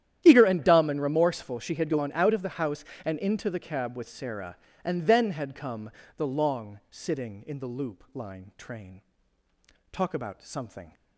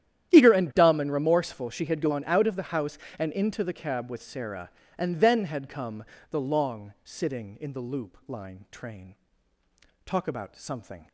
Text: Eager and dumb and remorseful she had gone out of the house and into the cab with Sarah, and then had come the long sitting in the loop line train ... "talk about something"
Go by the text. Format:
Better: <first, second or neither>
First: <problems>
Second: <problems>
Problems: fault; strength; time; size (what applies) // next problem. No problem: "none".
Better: neither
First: starts louder than the rest; strong; until 1.2 s; 11 dB // pauses between "come" and "the"; slight; at 5.8 s; 0.26 s long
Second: starts louder than the rest; strong; until 1.3 s; 11 dB // pauses between "come" and "the"; slight; at 6.0 s; 0.26 s long